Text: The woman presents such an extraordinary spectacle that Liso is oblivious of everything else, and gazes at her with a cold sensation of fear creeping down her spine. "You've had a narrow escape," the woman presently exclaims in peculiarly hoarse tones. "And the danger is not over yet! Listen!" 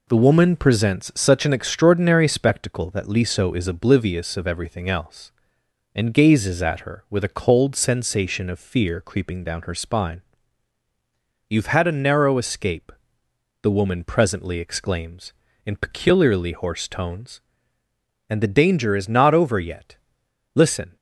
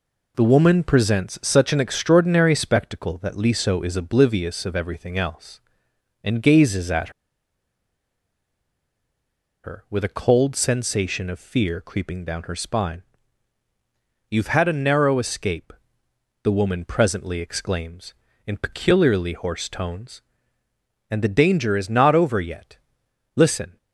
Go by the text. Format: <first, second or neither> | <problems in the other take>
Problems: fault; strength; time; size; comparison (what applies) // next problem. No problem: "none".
first | pauses between "at" and "her"; strong; at 7.0 s; 2.5 s long